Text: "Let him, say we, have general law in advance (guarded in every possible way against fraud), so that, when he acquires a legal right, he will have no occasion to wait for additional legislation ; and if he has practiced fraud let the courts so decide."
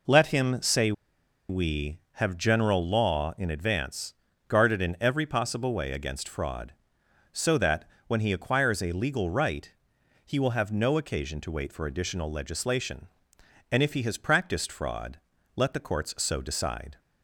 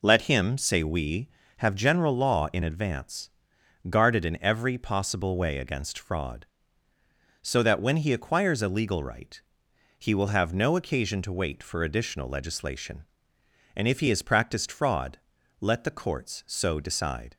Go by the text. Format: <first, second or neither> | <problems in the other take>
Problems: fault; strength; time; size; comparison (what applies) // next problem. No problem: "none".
second | pauses between "say" and "we"; noticeable; at 0.9 s; 0.57 s long // pauses between "fraud" and "let"; at 15.1 s; 0.38 s long; also in the second